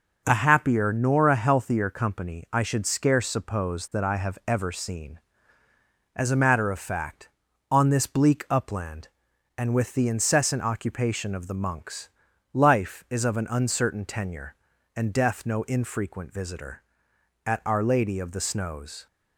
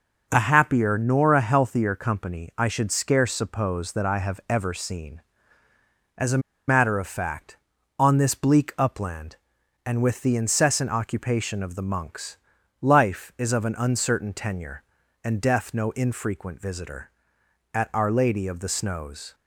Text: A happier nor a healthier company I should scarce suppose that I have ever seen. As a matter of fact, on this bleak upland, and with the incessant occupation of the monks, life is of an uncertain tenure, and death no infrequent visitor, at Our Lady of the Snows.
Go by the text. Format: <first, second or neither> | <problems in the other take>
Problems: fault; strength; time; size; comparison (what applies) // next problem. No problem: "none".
first | pauses between "a" and "matter"; slight; at 6.4 s; 0.28 s long